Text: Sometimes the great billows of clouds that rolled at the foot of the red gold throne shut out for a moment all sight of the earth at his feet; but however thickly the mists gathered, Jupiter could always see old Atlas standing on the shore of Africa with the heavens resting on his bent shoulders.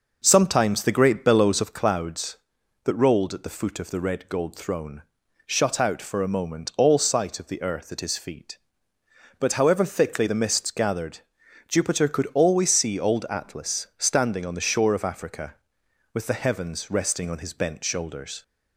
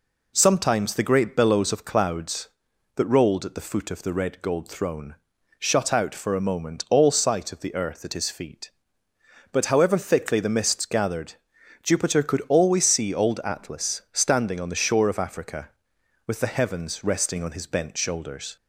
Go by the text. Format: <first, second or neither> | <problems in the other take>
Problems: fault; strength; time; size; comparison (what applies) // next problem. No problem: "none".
second | starts louder than the rest; noticeable; until 1.8 s; 5.5 dB // pauses between "throne" and "shut"; noticeable; at 5.0 s; 0.46 s long; noticeable in the second